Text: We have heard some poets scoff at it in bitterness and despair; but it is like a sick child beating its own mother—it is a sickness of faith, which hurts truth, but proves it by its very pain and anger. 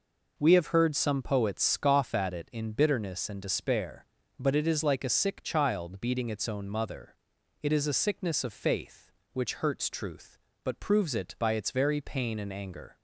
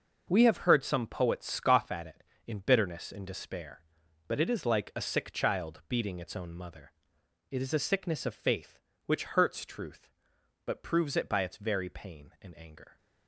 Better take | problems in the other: first | starts louder than the rest; noticeable; until 1.3 s; 6 dB // changes voice at "heard"; from 0.6 s on; 12.3 s long

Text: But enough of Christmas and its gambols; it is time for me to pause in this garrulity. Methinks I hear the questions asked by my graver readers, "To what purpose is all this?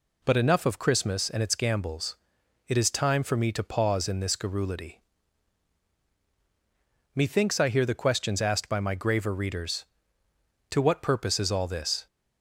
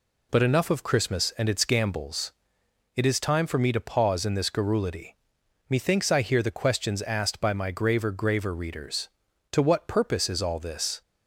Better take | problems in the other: first | says "graver" twice; at 8.1 s

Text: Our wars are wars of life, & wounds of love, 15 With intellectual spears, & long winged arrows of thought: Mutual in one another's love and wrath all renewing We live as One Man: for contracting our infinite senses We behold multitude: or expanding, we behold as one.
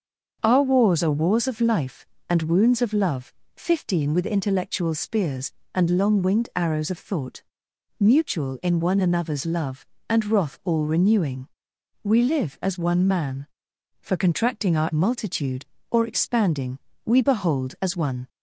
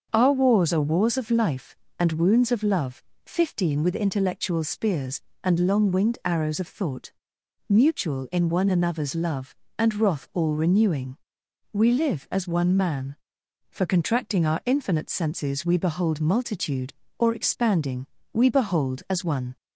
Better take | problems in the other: second | starts louder than the rest; until 1.4 s; 6.5 dB; also in the second // pauses between "renewing" and "We"; noticeable; at 11.4 s; 0.56 s long; noticeable in the second // skips "infinite senses We behold"; at 14.9 s

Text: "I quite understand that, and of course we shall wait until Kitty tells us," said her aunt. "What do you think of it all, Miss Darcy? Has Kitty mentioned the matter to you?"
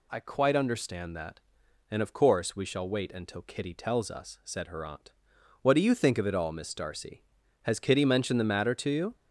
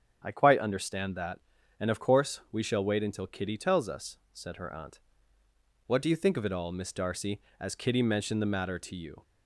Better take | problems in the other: first | starts louder than the rest; strong; until 1.2 s; 7.5 dB // says "As" for "Has"; at 7.5 s

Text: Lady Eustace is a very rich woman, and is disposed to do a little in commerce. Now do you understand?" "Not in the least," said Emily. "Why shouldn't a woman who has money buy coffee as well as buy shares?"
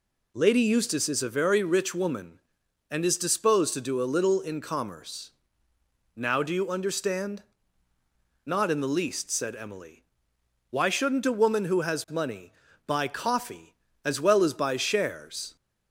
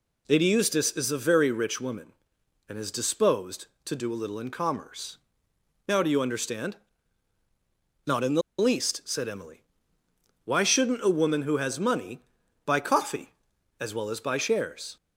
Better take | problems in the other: first | pauses between "the" and "least"; slight; at 8.4 s; 0.17 s long // pauses between "money" and "buy"; at 12.2 s; 0.40 s long; slight in the first

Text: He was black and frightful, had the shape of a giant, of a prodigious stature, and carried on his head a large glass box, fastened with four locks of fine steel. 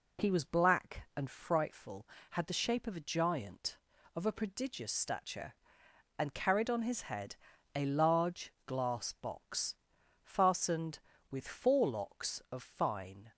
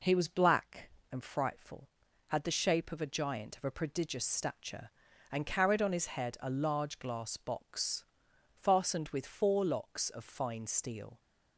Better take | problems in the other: second | pauses between "head" and "a"; at 7.3 s; 0.38 s long // stops before "steel"; at 13.3 s

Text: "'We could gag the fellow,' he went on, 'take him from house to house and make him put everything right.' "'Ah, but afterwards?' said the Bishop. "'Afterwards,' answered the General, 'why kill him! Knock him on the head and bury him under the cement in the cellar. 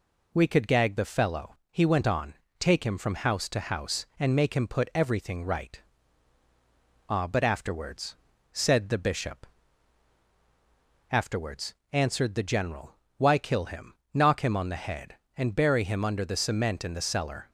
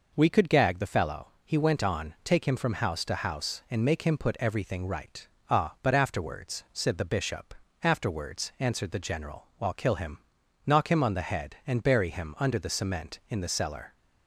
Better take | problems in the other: first | says "while" for "why"; at 9.5 s

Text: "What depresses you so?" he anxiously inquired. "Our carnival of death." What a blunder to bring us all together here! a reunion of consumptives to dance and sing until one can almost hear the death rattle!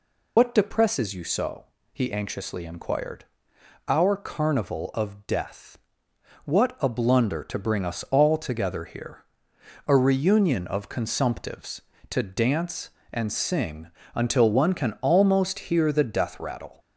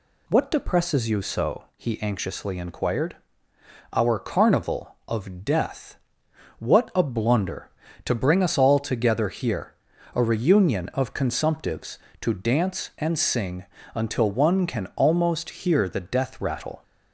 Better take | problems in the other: second | loses the start of "What"; at 0.3 s; 55 ms // pauses between "sing" and "until"; slight; at 13.8 s; 0.26 s long; slight in the second

